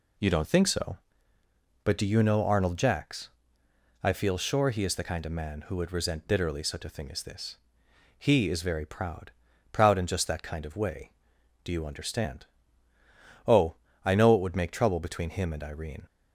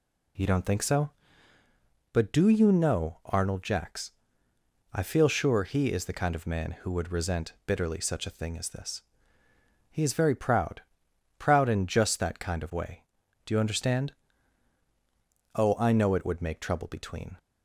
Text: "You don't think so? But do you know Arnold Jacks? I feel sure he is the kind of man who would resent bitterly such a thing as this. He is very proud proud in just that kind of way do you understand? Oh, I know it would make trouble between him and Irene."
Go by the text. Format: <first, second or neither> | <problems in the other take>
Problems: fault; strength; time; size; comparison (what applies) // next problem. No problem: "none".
first | pauses between "proud" and "proud"; noticeable; at 10.8 s; 0.56 s long; also in the first // stops before "him and Irene"; at 17.3 s